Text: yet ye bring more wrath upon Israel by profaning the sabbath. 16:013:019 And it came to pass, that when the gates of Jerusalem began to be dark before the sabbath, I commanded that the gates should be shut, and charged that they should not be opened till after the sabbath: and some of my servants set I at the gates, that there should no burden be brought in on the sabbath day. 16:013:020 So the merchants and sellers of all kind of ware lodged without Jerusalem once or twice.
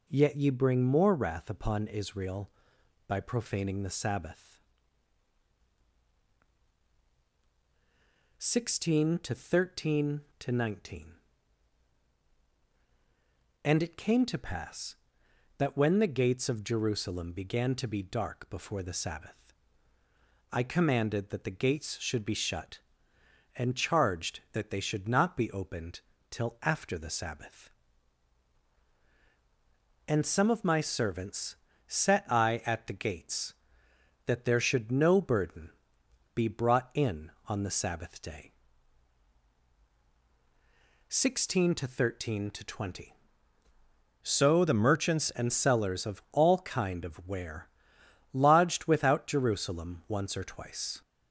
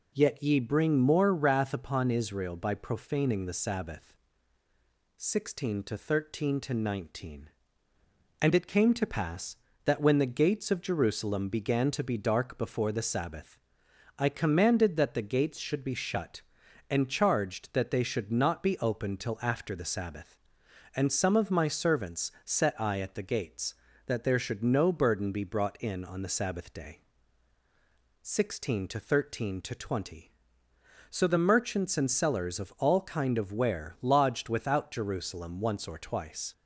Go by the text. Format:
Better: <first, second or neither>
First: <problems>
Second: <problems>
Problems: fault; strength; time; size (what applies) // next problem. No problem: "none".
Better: second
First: pauses between "opened" and "till"; slight; at 26.0 s; 0.28 s long // pauses between "servants" and "set"; slight; at 31.5 s; 0.32 s long // pauses between "burden" and "be"; noticeable; at 35.7 s; 0.64 s long // changes voice from "So" to "merchants"; from 44.2 to 45.3 s; 1.1 s long // pauses between "ware" and "lodged"; noticeable; at 47.6 s; 0.66 s long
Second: none